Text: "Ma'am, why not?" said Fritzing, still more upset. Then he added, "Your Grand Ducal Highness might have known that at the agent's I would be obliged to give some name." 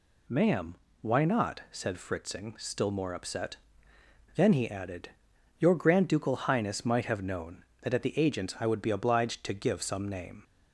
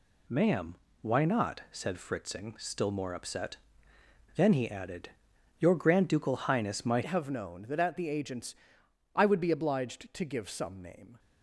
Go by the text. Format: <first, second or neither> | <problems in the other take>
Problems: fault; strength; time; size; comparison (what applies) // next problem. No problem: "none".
first | changes voice at "have"; from 7.0 s on; 4.1 s long // pauses between "agent's" and "I"; noticeable; at 8.5 s; 0.60 s long